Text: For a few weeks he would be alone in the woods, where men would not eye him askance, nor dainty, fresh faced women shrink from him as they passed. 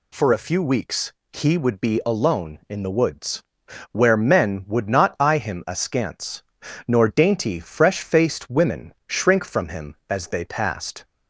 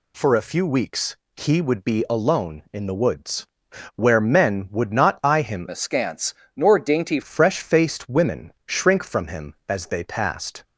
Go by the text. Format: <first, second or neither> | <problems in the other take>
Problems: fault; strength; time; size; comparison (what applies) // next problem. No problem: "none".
first | pauses between "weeks" and "he"; slight; at 1.1 s; 0.18 s long; slight in the first // changes voice from "askance" to "dainty"; from 5.7 to 7.2 s; 1.5 s long